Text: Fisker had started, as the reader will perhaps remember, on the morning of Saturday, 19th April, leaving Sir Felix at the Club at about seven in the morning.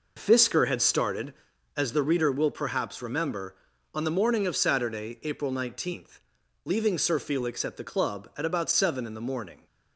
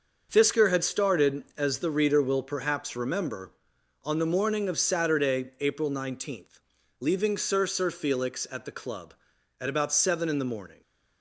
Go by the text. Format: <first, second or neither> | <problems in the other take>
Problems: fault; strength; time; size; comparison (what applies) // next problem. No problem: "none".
first | says "Sir" twice; at 7.6 s